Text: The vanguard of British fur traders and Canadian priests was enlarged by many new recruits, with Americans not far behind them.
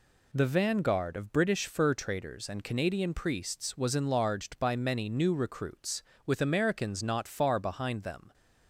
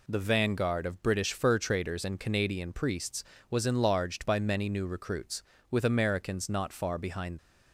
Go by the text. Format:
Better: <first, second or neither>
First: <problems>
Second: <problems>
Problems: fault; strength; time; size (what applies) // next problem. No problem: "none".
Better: first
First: none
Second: stops before "them"; at 7.3 s